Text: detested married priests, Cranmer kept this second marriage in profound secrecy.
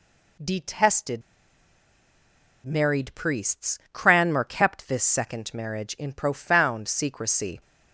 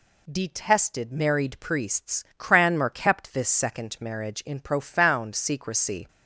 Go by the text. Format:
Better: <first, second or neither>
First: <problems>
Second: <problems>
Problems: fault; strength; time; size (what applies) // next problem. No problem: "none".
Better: second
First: pauses between "detested" and "married"; strong; at 1.2 s; 1.4 s long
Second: none